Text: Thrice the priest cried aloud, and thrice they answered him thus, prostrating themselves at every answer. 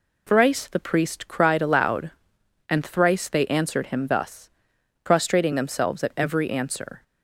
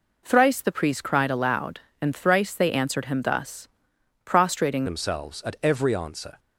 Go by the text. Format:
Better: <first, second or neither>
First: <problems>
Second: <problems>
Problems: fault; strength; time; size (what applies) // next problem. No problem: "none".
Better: first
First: none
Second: changes voice at "themselves"; from 4.8 s on; 1.5 s long